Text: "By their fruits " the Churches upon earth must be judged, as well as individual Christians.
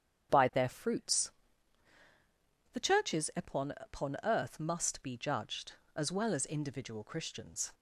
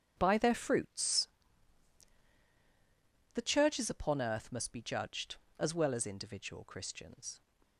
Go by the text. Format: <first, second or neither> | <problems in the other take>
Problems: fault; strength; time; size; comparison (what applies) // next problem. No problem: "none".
second | starts louder than the rest; strong; until 2.1 s; 7.5 dB; strong in the second // says "upon" twice; at 3.7 s